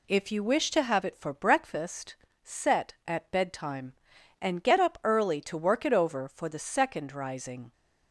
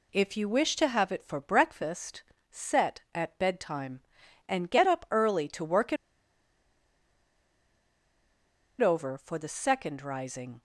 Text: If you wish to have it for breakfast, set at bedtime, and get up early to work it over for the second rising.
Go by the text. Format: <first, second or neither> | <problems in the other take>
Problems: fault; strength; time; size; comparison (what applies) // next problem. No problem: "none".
first | pauses between "it" and "over"; strong; at 5.9 s; 2.8 s long